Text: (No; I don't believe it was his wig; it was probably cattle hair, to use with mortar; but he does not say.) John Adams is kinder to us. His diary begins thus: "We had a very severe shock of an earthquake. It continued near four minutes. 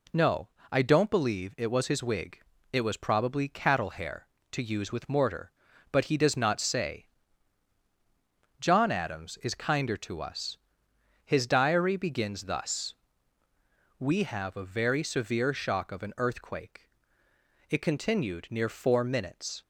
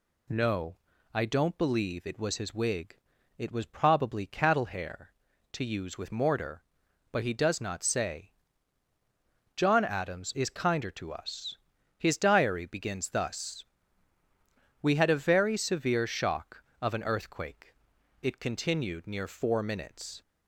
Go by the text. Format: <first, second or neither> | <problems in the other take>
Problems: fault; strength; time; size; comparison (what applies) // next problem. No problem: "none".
second | says "have" for "had"; at 14.2 s